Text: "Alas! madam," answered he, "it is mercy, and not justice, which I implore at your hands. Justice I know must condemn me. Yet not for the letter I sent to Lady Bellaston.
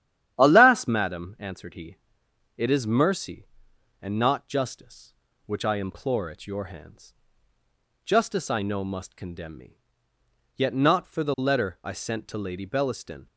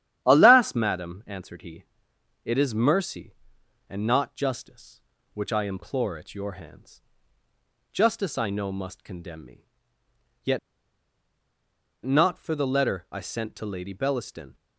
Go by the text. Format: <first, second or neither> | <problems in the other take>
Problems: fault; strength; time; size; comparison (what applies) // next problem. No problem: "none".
first | starts louder than the rest; strong; until 1.2 s; 10.5 dB; strong in the first // pauses between "Yet" and "not"; strong; at 10.5 s; 1.4 s long